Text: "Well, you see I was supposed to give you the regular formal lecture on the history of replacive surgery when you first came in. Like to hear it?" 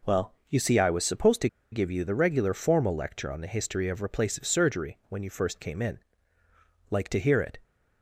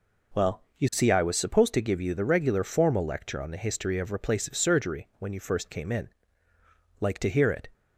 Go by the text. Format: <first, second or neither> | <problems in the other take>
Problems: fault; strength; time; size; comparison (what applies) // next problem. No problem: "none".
second | pauses between "to" and "give"; slight; at 1.4 s; 0.24 s long